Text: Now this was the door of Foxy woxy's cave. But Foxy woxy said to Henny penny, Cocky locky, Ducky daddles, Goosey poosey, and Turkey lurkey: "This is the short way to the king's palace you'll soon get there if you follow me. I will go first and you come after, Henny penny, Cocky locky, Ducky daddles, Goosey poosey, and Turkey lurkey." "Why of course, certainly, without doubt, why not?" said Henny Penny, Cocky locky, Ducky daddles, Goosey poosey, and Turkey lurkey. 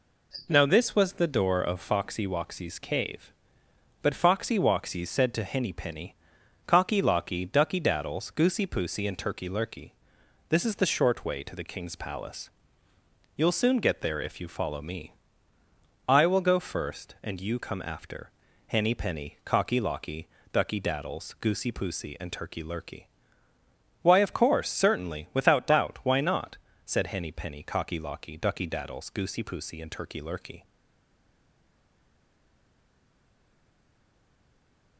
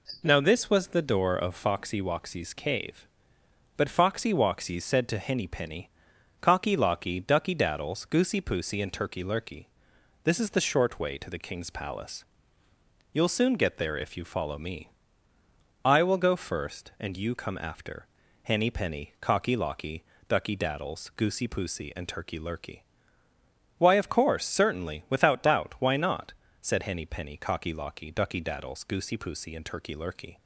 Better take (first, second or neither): second